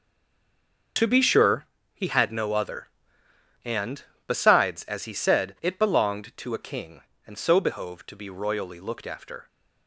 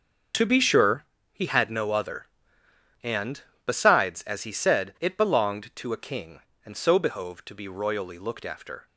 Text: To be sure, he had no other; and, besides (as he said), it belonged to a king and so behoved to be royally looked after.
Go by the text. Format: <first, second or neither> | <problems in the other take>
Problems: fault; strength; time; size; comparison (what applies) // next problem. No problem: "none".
second | stays silent before the first word; slight; until 0.9 s; 0.9 s long // starts louder than the rest; noticeable; until 2.2 s; 6 dB; noticeable in the second